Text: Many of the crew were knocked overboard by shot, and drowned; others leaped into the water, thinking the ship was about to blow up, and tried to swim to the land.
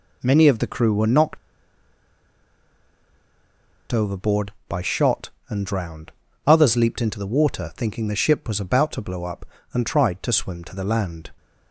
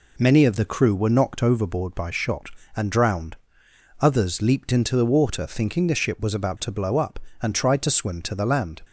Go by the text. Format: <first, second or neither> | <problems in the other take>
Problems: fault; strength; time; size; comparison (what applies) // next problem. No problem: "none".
second | pauses between "knocked" and "overboard"; strong; at 1.3 s; 2.5 s long